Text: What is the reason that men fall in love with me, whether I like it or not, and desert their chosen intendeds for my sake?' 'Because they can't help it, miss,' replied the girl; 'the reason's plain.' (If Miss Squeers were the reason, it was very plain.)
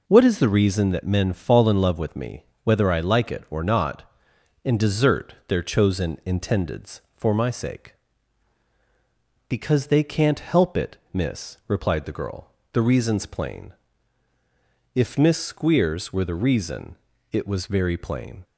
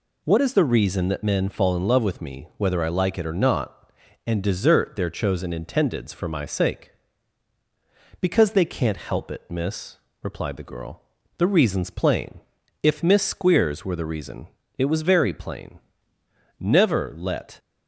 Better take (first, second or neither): first